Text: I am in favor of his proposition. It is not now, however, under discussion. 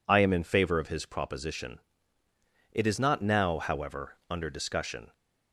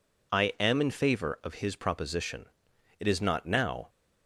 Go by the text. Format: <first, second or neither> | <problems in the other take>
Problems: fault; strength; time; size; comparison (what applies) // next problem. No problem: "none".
first | stops before "however under discussion"; at 3.8 s